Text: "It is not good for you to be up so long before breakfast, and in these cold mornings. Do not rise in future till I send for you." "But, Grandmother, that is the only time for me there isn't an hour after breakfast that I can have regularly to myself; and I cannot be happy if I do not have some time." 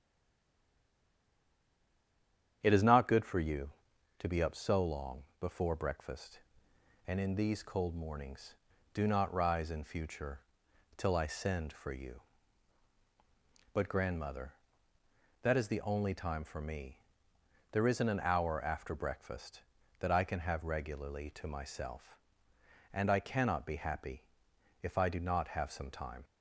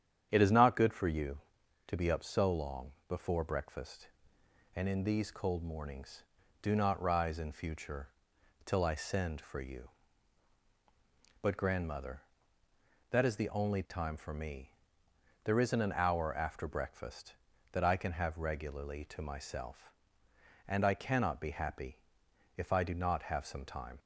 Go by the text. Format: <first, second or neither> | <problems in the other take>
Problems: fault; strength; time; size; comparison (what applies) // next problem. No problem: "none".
second | stays silent before the first word; strong; until 2.6 s; 2.6 s long // starts louder than the rest; strong; until 3.6 s; 9 dB; strong in the second // pauses between "long" and "before"; slight; at 5.2 s; 0.16 s long; slight in the second // pauses between "future" and "till"; noticeable; at 10.3 s; 0.58 s long; noticeable in the second // pauses between "me" and "there"; noticeable; at 16.9 s; 0.74 s long; noticeable in the second // pauses between "happy" and "if"; noticeable; at 24.2 s; 0.58 s long; noticeable in the second